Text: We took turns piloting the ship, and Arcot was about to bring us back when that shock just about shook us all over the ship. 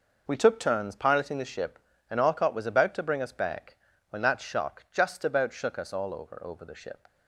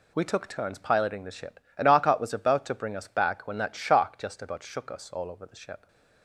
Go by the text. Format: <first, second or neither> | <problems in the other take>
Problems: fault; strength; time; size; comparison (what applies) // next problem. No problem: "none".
second | pauses between "back" and "when"; slight; at 3.7 s; 0.34 s long // says "over" twice; at 6.4 s